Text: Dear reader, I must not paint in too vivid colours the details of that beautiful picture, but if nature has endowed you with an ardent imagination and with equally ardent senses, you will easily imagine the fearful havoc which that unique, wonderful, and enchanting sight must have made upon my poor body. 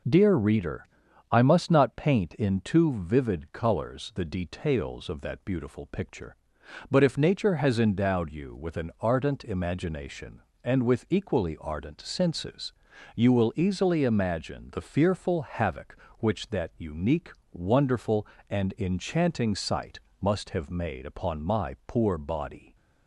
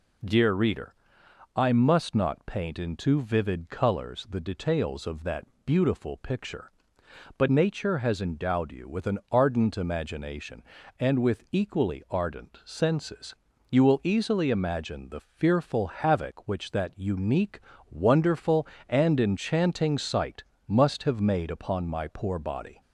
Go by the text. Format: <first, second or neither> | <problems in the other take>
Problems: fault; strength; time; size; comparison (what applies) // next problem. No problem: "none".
first | pauses between "that" and "beautiful"; slight; at 5.4 s; 0.18 s long // skips "if"; at 7.4 s // pauses between "sight" and "must"; slight; at 20.4 s; 0.22 s long; slight in the first